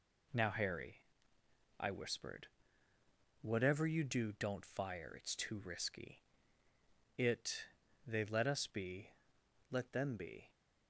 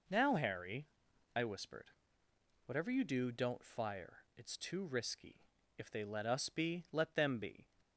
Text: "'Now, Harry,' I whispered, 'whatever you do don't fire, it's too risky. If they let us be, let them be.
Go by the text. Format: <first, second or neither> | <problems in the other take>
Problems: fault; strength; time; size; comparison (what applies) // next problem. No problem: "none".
second | says "It" for "If"; at 7.1 s